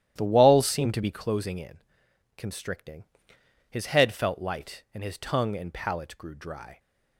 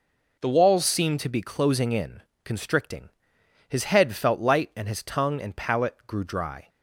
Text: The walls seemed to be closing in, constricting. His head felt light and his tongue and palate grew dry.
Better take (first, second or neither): second